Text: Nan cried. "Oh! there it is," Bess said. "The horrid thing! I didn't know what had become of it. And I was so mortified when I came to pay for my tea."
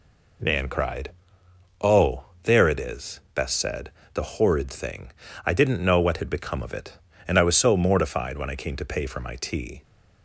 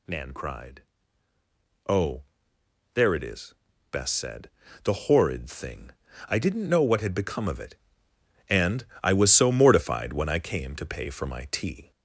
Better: first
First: none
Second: gets louder; slight; throughout; 3 dB // pauses between "And" and "I"; slight; at 8.8 s; 0.18 s long

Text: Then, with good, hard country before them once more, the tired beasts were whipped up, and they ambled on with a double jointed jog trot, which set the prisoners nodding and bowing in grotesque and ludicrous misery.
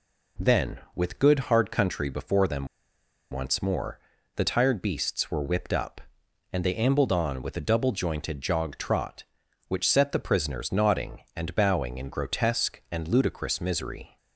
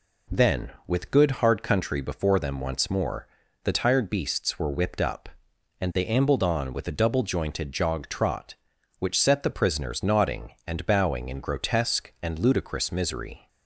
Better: second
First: pauses between "them" and "once"; noticeable; at 2.6 s; 0.65 s long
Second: none

